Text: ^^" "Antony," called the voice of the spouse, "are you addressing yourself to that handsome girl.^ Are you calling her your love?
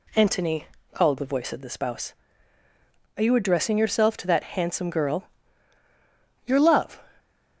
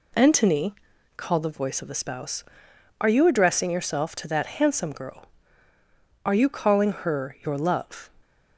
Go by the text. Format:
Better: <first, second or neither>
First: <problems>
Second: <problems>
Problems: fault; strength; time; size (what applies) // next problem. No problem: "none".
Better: second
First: skips "Are you calling her"; at 5.8 s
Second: none